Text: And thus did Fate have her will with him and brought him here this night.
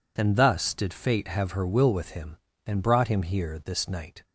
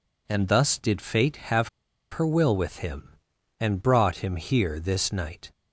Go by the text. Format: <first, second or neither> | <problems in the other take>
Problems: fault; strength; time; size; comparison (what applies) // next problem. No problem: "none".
first | pauses between "have" and "her"; at 1.6 s; 0.42 s long